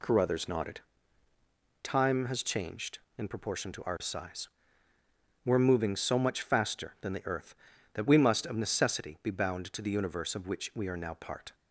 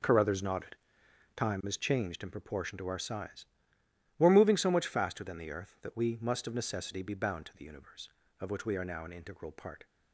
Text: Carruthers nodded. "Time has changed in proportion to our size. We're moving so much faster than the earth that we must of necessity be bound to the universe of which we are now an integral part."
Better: second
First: skips "an integral"; at 11.1 s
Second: none

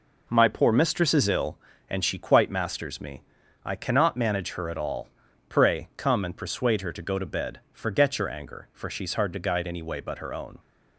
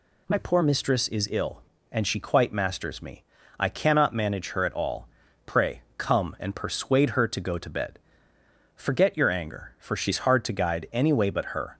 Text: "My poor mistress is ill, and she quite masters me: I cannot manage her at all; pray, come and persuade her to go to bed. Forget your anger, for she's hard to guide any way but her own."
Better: first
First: none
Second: stops before "own"; at 11.7 s

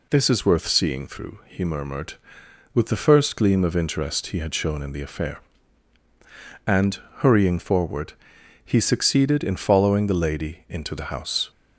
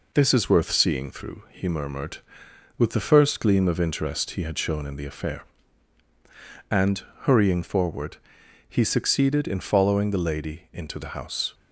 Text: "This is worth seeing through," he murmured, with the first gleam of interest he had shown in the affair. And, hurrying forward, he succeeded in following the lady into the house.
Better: first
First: none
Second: gets quieter; slight; throughout; 2.5 dB

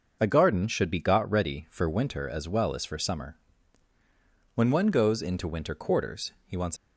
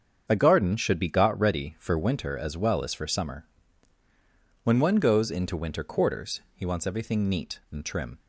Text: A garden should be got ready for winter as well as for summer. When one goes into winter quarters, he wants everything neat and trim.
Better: second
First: starts louder than the rest; noticeable; until 1.2 s; 6 dB // stops before "everything neat and trim"; at 6.7 s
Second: starts louder than the rest; strong; until 1.3 s; 7.5 dB

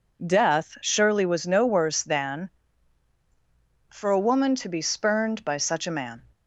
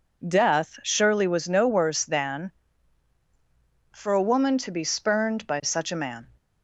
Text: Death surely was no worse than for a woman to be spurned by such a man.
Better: neither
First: none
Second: none

